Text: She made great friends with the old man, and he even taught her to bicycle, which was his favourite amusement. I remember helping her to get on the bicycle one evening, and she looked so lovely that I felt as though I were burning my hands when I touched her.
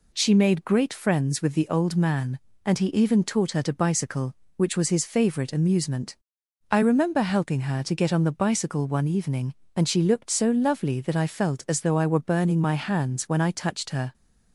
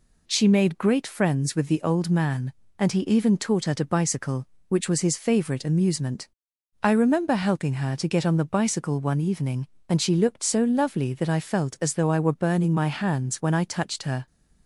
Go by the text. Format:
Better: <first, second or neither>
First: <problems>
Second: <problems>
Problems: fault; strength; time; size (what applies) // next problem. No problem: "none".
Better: neither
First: none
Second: none